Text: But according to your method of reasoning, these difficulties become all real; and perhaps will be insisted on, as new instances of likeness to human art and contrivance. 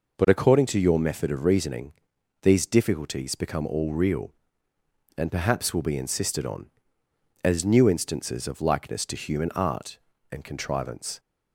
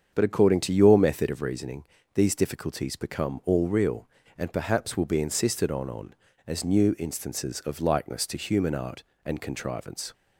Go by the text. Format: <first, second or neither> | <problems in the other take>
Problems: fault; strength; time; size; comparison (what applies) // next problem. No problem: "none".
first | starts louder than the rest; strong; until 1.1 s; 7.5 dB // says "on" twice; at 5.8 s